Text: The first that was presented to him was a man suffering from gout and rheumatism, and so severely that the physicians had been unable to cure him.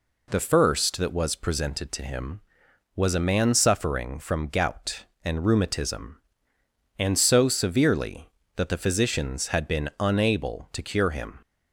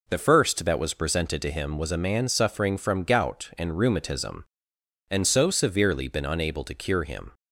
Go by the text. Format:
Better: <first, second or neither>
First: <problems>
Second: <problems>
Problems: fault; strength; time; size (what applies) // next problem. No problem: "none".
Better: first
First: none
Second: skips "that the physicians had"; at 6.0 s